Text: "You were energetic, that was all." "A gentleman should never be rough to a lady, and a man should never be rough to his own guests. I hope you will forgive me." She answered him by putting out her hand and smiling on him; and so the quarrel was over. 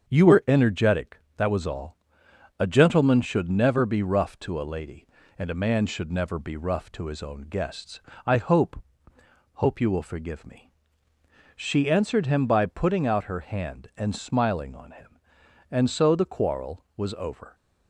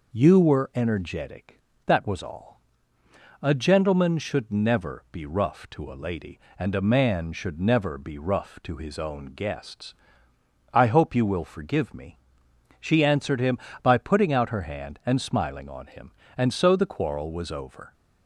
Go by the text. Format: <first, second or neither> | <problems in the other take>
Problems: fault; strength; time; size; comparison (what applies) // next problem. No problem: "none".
second | starts louder than the rest; strong; until 1.1 s; 7 dB // says "hope" twice; at 9.5 s